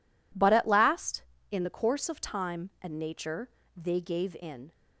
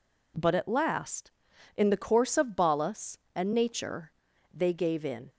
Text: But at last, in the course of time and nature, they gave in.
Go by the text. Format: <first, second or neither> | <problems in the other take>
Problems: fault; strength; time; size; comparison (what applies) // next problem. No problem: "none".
first | says "balas" for "time"; at 2.5 s